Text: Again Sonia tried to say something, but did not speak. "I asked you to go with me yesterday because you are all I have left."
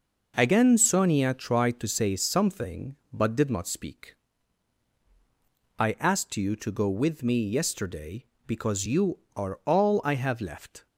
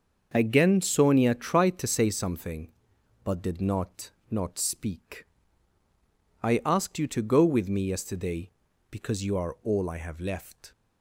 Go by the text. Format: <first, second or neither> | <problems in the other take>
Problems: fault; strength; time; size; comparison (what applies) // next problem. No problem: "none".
first | starts louder than the rest; until 1.3 s; 6.5 dB // says "not" twice; at 4.3 s